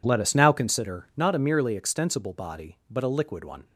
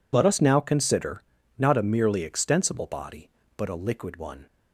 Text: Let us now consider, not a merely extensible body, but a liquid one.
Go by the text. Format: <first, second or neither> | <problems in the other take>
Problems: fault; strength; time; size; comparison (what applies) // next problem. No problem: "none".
neither | none